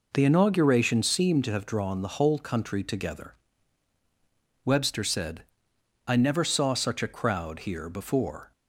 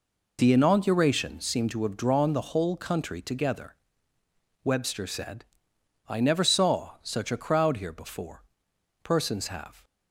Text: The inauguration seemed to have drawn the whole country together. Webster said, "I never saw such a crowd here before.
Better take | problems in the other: first | goes on to say "Persons have"; noticeable; from 9.0 s on; 0.80 s long

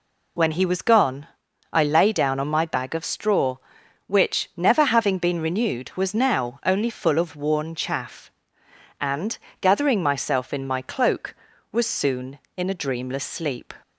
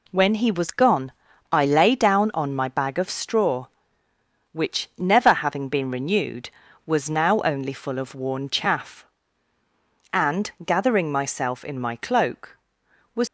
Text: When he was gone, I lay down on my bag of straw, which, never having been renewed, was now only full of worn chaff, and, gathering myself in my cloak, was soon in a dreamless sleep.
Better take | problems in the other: first | stops before "soon in a dreamless sleep"; at 13.2 s

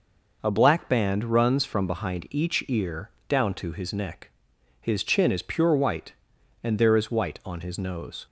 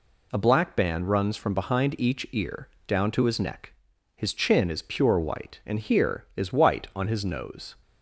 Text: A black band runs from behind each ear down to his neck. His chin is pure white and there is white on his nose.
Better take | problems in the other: first | pauses between "ear" and "down"; slight; at 2.6 s; 0.20 s long; slight in the first // says "here" for "there"; at 5.7 s

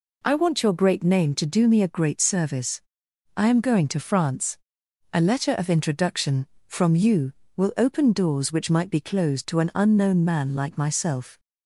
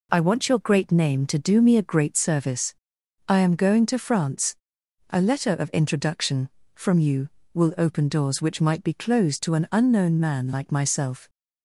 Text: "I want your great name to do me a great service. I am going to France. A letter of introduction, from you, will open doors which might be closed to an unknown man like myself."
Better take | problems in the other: neither | none

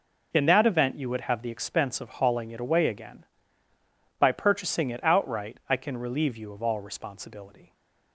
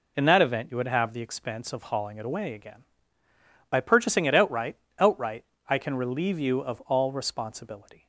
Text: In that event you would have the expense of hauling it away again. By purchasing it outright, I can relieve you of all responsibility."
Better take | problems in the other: first | says "outright" twice; at 4.9 s

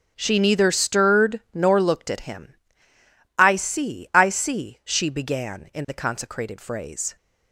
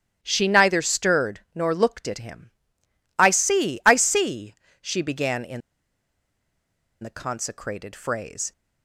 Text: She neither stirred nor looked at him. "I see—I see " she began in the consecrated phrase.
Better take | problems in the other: first | starts louder than the rest; strong; until 1.2 s; 10 dB; also in the first // pauses between "in" and "the"; strong; at 5.6 s; 1.4 s long

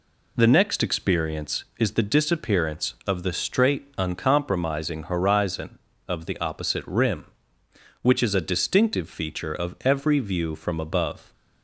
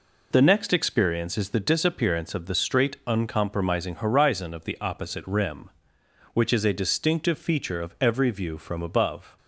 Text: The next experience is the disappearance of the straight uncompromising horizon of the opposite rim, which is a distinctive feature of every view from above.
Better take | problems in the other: neither | none

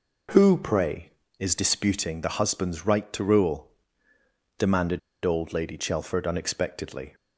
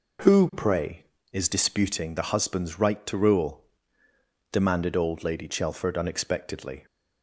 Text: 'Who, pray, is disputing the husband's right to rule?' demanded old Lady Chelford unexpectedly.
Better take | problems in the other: second | pauses between "demanded" and "old"; slight; at 4.9 s; 0.24 s long

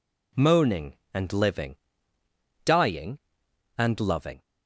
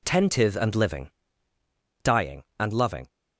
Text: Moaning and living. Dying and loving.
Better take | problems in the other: first | says "Tentive" for "Moaning"; at 0.0 s

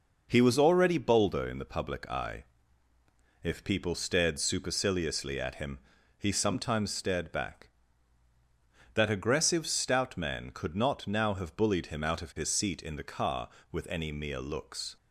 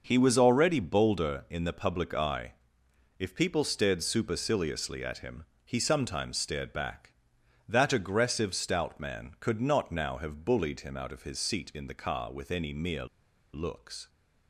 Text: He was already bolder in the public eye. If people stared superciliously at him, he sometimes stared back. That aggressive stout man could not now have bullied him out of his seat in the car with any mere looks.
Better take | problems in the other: first | pauses between "mere" and "looks"; noticeable; at 13.0 s; 0.48 s long

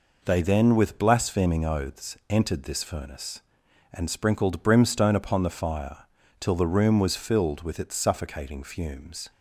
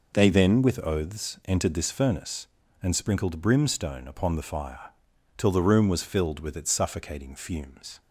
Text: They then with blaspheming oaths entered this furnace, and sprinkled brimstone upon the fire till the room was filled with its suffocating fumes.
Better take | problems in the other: first | skips "blaspheming"; at 0.8 s // pauses between "fire" and "till"; noticeable; at 4.9 s; 0.48 s long; slight in the first

